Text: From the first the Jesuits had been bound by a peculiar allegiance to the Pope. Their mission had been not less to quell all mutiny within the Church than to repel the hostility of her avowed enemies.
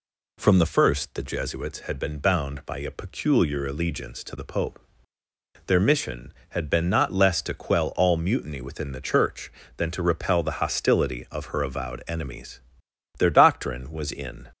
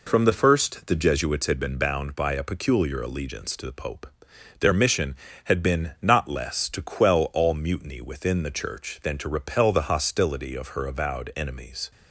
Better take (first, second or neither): second